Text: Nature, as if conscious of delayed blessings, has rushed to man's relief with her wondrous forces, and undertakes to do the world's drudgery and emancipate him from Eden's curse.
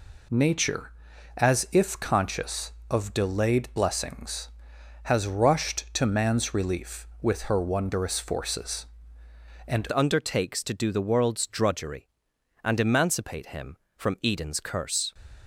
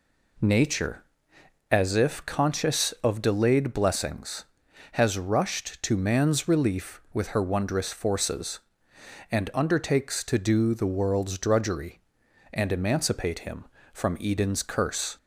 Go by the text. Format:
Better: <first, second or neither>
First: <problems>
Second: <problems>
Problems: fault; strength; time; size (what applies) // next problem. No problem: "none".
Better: second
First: changes voice at "undertakes"; from 9.9 s on; 5.2 s long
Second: none